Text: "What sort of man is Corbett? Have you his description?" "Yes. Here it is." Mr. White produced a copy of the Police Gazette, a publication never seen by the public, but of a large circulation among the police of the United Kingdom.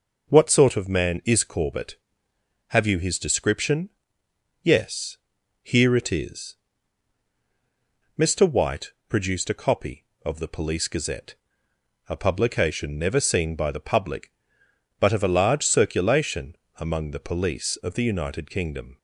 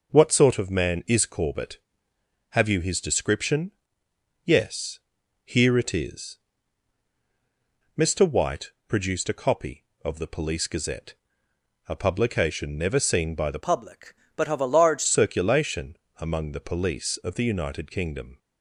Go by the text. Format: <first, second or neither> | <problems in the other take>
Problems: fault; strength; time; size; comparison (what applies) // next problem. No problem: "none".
first | pauses between "White" and "produced"; slight; at 8.7 s; 0.16 s long; slight in the first // changes voice from "public" to "large"; from 13.6 to 15.0 s; 1.4 s long // pauses between "circulation" and "among"; slight; at 15.9 s; 0.20 s long; slight in the first